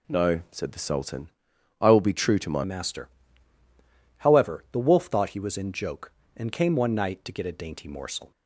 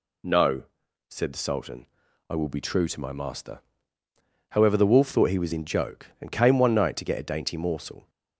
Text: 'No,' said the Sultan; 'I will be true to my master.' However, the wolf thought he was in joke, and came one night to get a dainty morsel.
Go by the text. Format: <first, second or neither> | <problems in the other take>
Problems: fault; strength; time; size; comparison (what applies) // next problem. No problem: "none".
second | changes voice at "master"; from 2.6 s on; 5.7 s long